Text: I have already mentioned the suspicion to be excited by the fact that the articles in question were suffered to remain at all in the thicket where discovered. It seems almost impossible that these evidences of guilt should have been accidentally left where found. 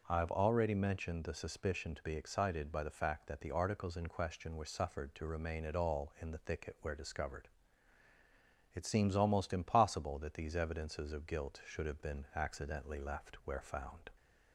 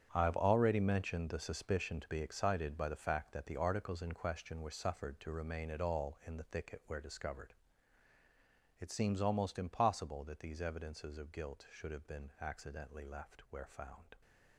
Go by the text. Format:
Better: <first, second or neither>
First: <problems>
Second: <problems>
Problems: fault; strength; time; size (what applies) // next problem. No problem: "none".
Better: first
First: none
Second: gets quieter; strong; throughout; 12.5 dB